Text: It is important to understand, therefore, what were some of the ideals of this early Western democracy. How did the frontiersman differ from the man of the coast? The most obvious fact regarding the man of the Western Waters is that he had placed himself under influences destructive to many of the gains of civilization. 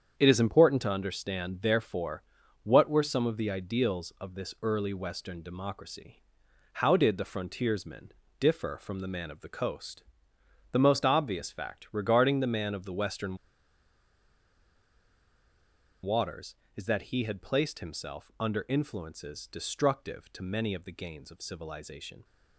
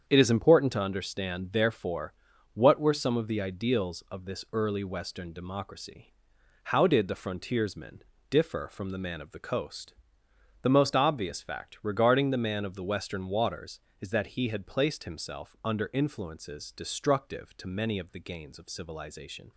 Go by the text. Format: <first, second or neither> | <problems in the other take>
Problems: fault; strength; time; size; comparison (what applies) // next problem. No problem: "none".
second | starts louder than the rest; strong; until 1.2 s; 8 dB; strong in the second // pauses between "frontiersman" and "differ"; slight; at 8.1 s; 0.28 s long; slight in the second // pauses between "Western" and "Waters"; strong; at 13.3 s; 2.6 s long